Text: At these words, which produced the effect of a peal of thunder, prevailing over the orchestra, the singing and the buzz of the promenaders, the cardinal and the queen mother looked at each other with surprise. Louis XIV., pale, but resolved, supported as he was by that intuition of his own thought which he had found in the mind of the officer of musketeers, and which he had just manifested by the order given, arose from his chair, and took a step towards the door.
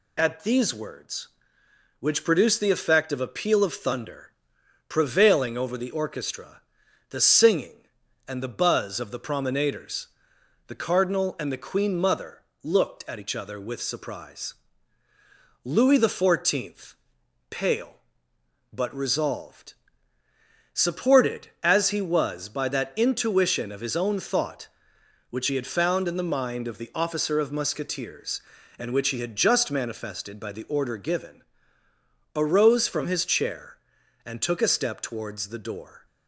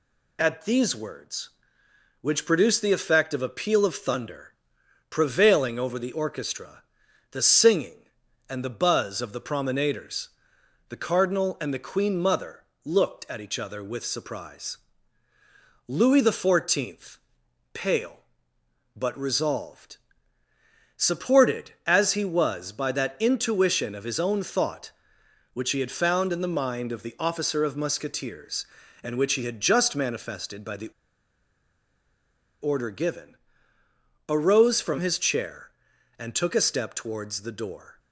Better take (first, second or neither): first